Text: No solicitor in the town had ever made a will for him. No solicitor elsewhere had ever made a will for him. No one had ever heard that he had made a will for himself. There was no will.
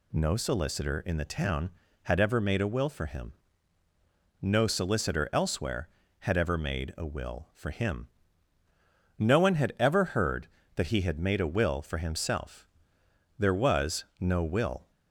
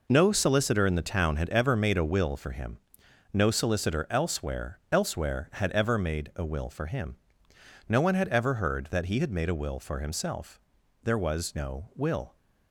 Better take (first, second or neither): first